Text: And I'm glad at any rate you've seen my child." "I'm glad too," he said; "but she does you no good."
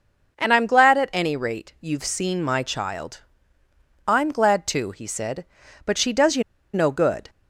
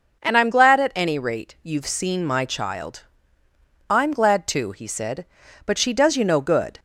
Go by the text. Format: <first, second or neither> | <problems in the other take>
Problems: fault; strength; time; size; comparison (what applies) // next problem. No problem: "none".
second | pauses between "you" and "no"; slight; at 6.4 s; 0.31 s long